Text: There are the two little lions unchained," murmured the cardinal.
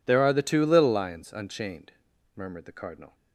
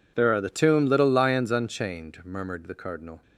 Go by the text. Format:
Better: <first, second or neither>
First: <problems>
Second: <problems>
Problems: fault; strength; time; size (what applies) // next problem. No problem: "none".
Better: first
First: none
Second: says "tomb" for "two"; at 0.4 s